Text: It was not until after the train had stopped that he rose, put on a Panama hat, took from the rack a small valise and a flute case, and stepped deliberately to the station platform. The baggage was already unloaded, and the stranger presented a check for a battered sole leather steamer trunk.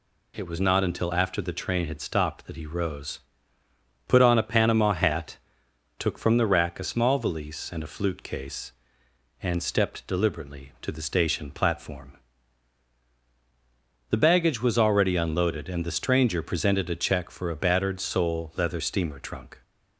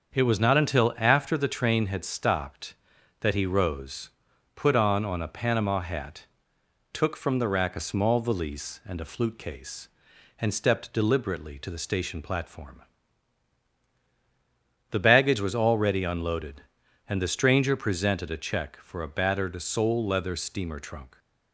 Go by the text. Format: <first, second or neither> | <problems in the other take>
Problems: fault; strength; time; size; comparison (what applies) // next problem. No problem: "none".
first | starts louder than the rest; until 1.1 s; 7 dB // says "on" twice; at 5.0 s